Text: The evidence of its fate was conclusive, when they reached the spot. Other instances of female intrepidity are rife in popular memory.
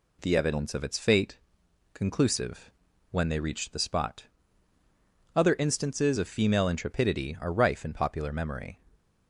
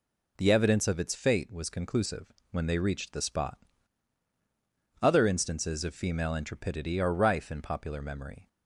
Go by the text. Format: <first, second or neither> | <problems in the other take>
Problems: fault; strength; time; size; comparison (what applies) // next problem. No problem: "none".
second | skips "was"; at 1.6 s